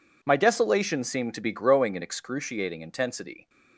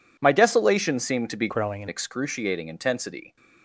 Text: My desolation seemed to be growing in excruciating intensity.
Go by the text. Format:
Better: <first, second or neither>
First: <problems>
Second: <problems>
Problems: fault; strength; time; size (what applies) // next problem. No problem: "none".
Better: first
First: none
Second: changes voice from "growing" to "in"; from 1.4 to 1.8 s; 0.4 s long